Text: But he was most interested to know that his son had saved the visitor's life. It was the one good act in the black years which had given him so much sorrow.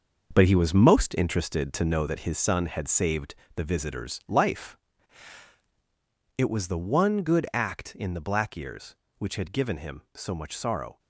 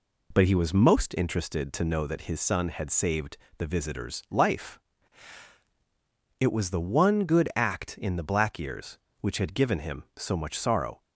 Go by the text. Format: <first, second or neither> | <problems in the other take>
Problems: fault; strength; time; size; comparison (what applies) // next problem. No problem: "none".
second | gets quieter; strong; throughout; 9 dB // pauses between "saved" and "the"; slight; at 3.3 s; 0.20 s long; slight in the second